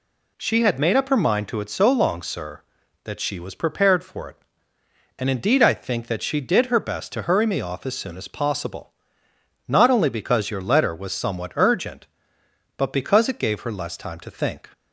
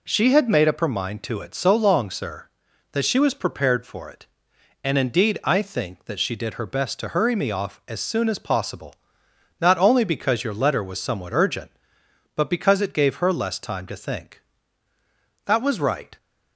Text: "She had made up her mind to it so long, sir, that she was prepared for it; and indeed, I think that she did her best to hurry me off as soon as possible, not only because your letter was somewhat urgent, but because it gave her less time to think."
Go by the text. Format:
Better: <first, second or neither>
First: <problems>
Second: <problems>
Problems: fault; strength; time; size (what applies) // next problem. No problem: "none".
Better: first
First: none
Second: goes on to say "That was right"; noticeable; from 15.4 s on; 0.72 s long